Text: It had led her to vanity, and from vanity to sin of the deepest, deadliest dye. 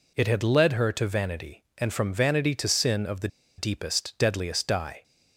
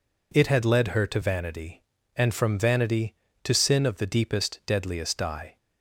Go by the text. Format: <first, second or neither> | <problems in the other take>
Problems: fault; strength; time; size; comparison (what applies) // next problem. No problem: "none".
second | pauses between "the" and "deepest"; slight; at 3.2 s; 0.30 s long